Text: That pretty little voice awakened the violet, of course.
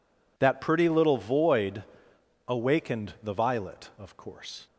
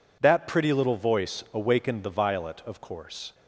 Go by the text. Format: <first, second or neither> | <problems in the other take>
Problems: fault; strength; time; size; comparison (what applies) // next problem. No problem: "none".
second | says "void" for "voice"; at 1.1 s